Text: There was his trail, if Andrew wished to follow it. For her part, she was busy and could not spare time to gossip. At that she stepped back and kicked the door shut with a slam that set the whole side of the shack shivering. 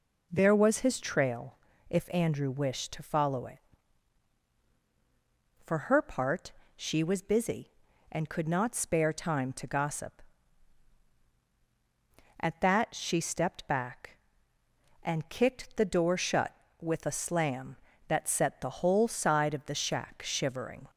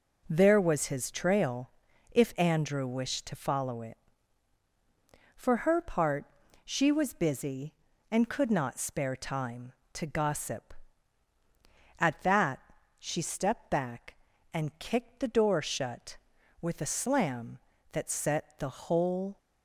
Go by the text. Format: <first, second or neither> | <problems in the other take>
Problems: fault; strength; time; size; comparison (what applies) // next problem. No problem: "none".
first | pauses between "that" and "she"; at 12.5 s; 0.40 s long // stops before "side of the shack shivering"; at 19.3 s